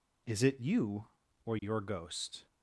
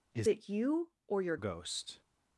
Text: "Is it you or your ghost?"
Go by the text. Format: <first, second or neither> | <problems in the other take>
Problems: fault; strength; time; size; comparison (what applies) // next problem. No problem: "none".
first | changes voice from "it" to "your"; from 0.2 to 1.3 s; 1.1 s long